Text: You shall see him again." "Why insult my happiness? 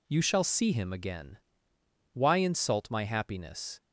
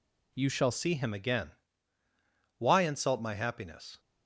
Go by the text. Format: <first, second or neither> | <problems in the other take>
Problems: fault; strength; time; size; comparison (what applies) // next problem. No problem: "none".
first | changes voice at "see"; from 0.7 s on; 3.2 s long